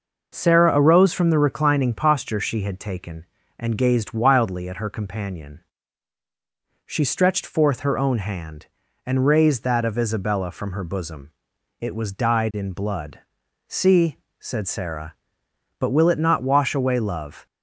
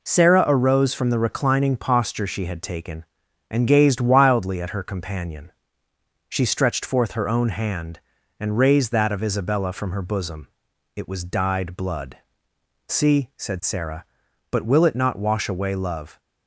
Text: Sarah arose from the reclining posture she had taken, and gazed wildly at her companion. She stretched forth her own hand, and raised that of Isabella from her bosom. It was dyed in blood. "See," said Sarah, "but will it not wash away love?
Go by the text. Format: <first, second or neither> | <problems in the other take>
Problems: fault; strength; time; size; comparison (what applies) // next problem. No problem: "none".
first | skips "in"; at 11.7 s